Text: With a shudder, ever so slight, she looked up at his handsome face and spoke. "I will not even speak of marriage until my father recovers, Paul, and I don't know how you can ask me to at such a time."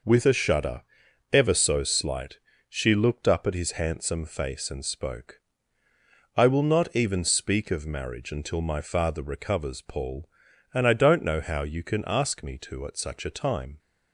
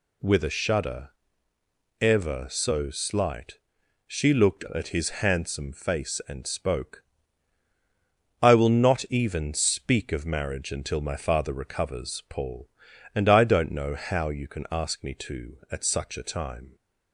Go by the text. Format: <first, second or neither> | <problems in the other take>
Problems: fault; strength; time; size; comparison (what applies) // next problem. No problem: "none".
first | skips "up"; at 4.7 s